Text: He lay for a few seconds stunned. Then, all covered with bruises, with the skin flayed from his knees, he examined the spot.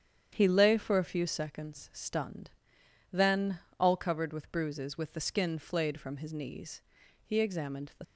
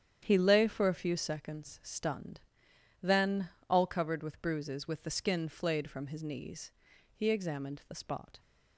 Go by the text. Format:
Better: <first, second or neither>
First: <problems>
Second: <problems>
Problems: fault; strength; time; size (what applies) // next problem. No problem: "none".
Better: second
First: starts louder than the rest; strong; until 1.3 s; 9 dB // stops before "spot"; at 8.0 s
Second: starts louder than the rest; strong; until 1.2 s; 9 dB